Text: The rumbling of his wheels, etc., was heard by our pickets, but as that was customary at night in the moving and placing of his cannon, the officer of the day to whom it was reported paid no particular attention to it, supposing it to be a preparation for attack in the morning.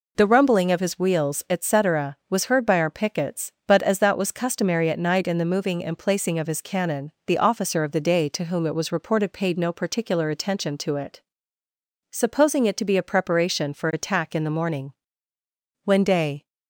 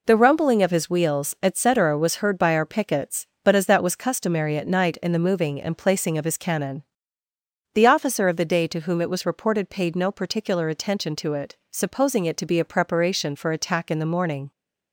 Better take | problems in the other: second | goes on to say "When day"; noticeable; from 15.8 s on; 0.62 s long

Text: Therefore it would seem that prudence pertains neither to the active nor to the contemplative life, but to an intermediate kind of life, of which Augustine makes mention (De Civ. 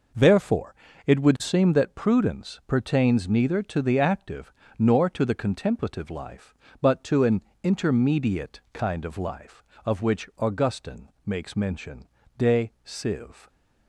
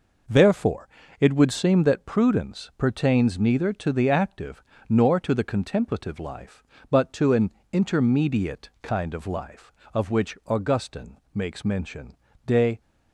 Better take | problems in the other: first | pauses between "Therefore" and "it"; slight; at 0.8 s; 0.30 s long; slight in the first // pauses between "active" and "nor"; slight; at 4.6 s; 0.24 s long; slight in the first // pauses between "an" and "intermediate"; slight; at 7.5 s; 0.20 s long; slight in the first // pauses between "Augustine" and "makes"; slight; at 11.1 s; 0.16 s long; slight in the first // stops before "Civ"; at 12.8 s

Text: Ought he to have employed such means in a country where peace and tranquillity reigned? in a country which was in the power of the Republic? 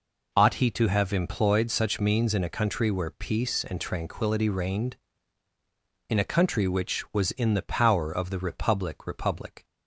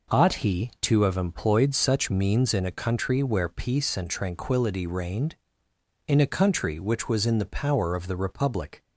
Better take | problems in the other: second | says "Republic" twice; at 9.0 s

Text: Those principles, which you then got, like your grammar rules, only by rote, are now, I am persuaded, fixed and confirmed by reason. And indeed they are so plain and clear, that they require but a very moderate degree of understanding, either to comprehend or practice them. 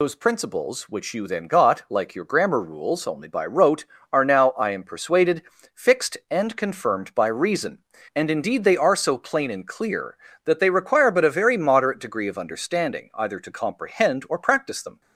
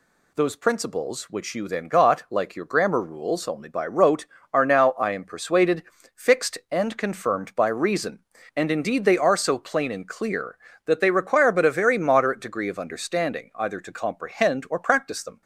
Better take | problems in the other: second | loses the start of "Those"; at 0.0 s; 60 ms

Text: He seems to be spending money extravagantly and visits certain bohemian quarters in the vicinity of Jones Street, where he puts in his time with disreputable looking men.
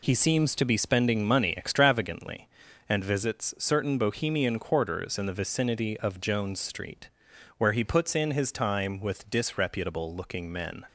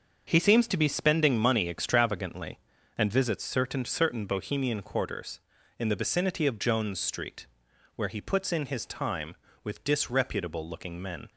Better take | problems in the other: first | starts louder than the rest; until 1.2 s; 6.5 dB // says "certain" twice; at 3.8 s

